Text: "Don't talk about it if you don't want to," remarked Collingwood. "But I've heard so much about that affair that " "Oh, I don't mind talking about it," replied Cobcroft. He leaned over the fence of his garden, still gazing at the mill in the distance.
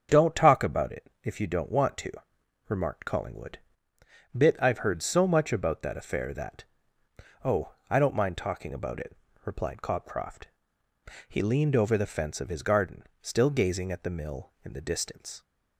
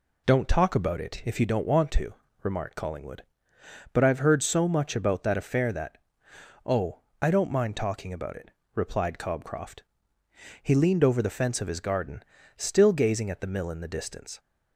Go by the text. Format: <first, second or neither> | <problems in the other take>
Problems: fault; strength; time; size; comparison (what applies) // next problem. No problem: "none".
second | starts louder than the rest; strong; until 1.2 s; 7.5 dB // says "Bit" for "But"; at 4.3 s